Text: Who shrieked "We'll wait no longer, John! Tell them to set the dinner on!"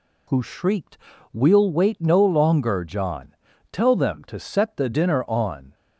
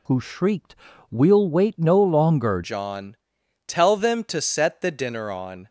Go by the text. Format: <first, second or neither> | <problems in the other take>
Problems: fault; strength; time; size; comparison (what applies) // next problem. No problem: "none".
first | pauses between "shrieked" and "We'll"; slight; at 0.7 s; 0.34 s long; slight in the first // changes voice at "John"; from 2.6 s on; 3.0 s long